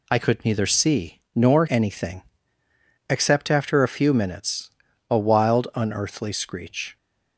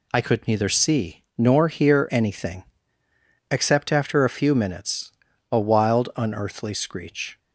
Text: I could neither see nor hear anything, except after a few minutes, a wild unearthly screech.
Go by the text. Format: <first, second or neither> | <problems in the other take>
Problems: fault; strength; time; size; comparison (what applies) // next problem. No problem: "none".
second | skips "hear"; at 1.6 s